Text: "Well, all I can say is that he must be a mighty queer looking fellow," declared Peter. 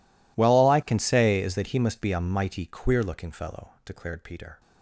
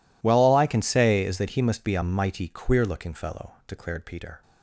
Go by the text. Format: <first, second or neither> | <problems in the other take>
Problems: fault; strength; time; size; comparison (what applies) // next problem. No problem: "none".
second | gets quieter; strong; throughout; 28 dB